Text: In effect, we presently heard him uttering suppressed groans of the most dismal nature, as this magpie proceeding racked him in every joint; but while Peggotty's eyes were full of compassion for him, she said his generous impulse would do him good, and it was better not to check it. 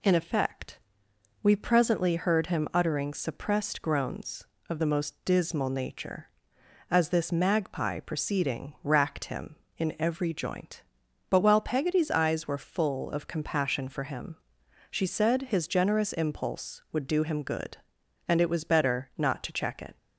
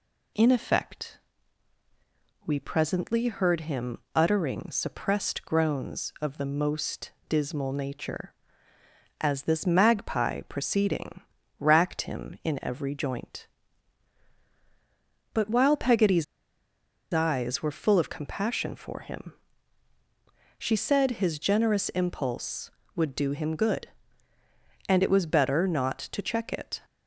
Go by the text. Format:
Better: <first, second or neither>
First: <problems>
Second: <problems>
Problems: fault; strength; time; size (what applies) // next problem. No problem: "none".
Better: first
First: none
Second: pauses between "him" and "uttering"; slight; at 3.9 s; 0.16 s long // pauses between "most" and "dismal"; slight; at 7.1 s; 0.16 s long // pauses between "proceeding" and "racked"; at 11.2 s; 0.38 s long // pauses between "Peggotty's" and "eyes"; noticeable; at 16.2 s; 0.88 s long